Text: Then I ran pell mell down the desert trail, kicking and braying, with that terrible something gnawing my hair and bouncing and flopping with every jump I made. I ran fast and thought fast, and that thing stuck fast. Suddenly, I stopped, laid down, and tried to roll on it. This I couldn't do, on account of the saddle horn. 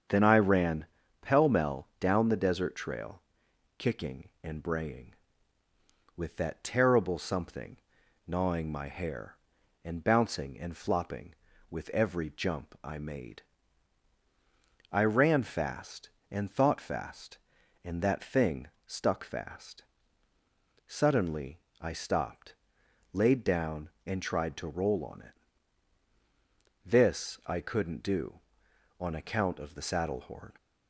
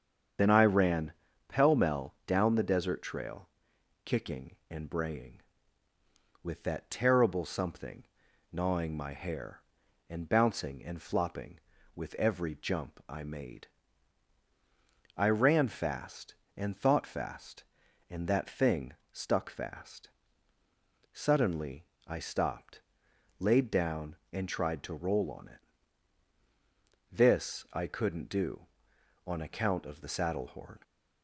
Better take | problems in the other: first | loses the start of "Then"; at 0.3 s; 30 ms // starts louder than the rest; strong; until 1.7 s; 7.5 dB; strong in the first // pauses between "ran" and "pell"; slight; at 1.1 s; 0.36 s long; slight in the first // pauses between "something" and "gnawing"; noticeable; at 8.0 s; 0.46 s long; noticeable in the first // pauses between "thing" and "stuck"; slight; at 18.9 s; 0.18 s long; slight in the first

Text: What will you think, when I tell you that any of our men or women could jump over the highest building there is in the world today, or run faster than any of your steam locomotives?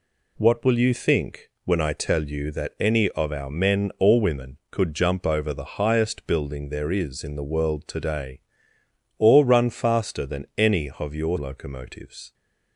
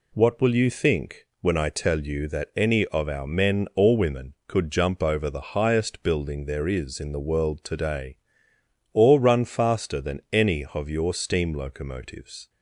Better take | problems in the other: second | skips "steam"; at 11.3 s

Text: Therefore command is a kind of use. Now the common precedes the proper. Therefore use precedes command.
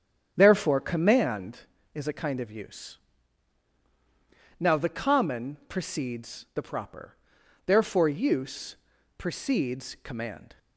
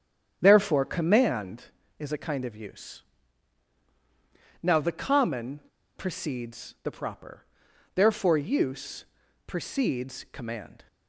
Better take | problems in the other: first | starts louder than the rest; strong; until 1.4 s; 9 dB; strong in the first // pauses between "common" and "precedes"; slight; at 5.6 s; 0.36 s long // pauses between "use" and "precedes"; at 9.0 s; 0.42 s long; also in the first

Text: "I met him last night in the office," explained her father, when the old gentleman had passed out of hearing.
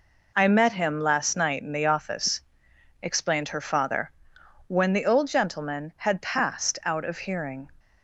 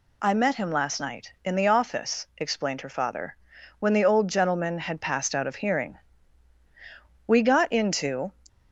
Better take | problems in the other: first | goes on to say "We got into"; noticeable; from 7.2 s on; 1.0 s long

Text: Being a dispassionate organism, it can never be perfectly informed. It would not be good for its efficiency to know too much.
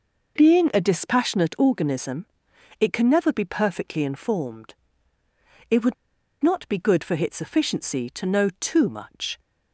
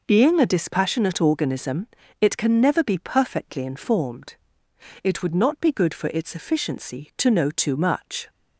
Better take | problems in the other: second | pauses between "would" and "not"; noticeable; at 5.9 s; 0.48 s long

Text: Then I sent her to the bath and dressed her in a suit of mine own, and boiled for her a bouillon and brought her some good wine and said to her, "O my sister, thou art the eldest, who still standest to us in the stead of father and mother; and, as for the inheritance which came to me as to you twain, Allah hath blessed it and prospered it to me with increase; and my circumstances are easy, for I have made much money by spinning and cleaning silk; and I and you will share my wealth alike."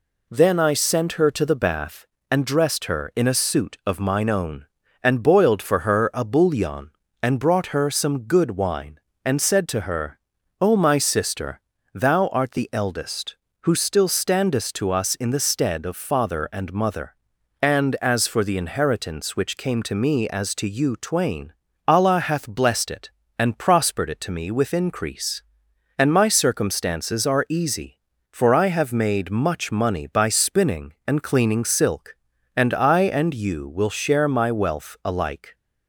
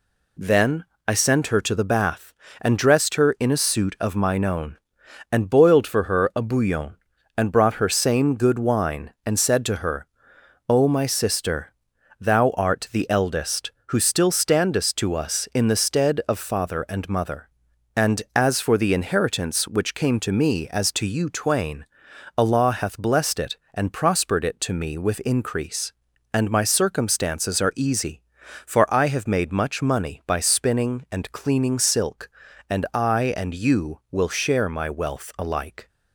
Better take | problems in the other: first | pauses between "Then" and "I"; slight; at 0.8 s; 0.24 s long // says "same" for "some"; at 7.8 s

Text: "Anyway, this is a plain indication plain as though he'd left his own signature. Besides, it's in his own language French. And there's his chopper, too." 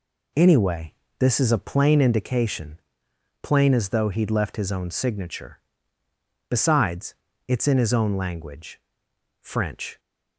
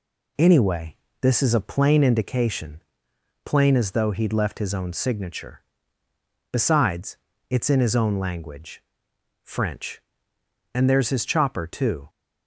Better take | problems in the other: second | pauses between "indication" and "plain"; noticeable; at 2.7 s; 0.64 s long; noticeable in the second // pauses between "language" and "French"; noticeable; at 8.8 s; 0.60 s long; noticeable in the second // stops before "And there's his chopper too"; at 9.9 s

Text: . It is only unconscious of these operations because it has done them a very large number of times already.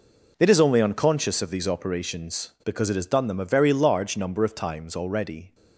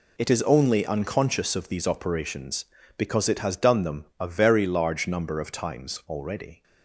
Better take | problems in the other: neither | none

